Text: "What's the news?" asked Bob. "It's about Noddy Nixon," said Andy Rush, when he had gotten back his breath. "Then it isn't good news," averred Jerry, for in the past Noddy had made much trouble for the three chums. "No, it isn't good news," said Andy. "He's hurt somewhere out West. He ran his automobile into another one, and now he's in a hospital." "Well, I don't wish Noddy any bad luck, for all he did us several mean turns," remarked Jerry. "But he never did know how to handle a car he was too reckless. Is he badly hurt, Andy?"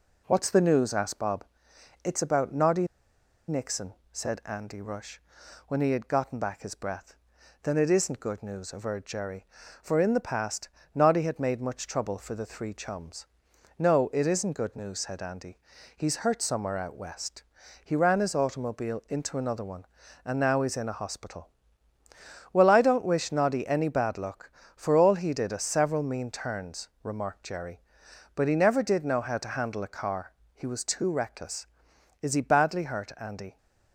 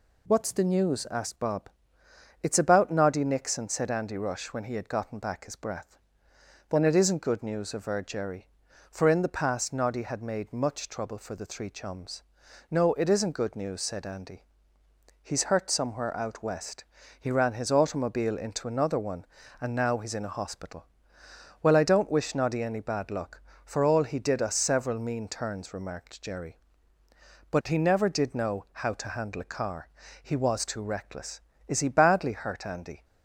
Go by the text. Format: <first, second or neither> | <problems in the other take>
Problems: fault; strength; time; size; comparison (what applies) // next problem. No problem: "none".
second | pauses between "Noddy" and "Nixon"; noticeable; at 2.8 s; 0.61 s long // pauses between "past" and "Noddy"; slight; at 10.6 s; 0.24 s long // pauses between "car" and "he"; slight; at 30.3 s; 0.26 s long; slight in the second